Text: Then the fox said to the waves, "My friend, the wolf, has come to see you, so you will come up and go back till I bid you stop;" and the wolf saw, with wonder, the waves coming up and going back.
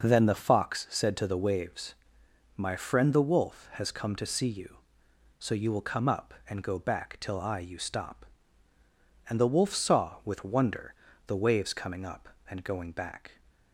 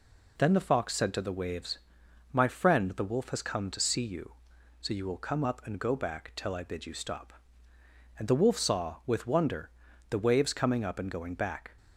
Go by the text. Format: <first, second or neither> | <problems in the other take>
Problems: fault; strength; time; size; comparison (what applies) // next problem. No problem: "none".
second | skips "bid"; at 7.5 s